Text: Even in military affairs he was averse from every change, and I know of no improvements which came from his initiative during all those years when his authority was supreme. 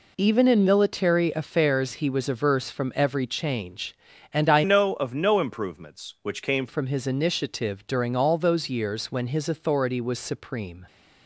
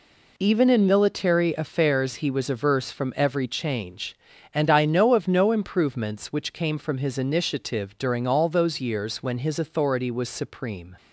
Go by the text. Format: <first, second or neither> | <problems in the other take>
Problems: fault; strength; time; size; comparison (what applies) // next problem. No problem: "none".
second | changes voice from "know" to "came"; from 4.6 to 6.6 s; 2.0 s long